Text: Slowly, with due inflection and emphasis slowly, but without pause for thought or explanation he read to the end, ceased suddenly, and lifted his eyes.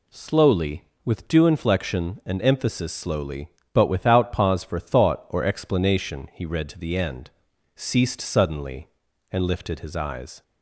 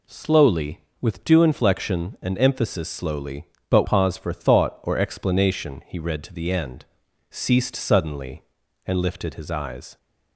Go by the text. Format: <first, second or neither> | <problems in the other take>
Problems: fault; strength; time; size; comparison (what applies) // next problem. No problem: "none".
first | skips "without"; at 3.8 s